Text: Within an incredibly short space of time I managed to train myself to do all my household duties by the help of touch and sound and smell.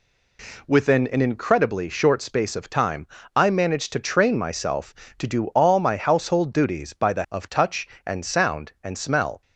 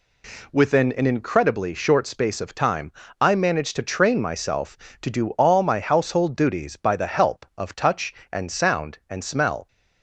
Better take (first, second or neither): second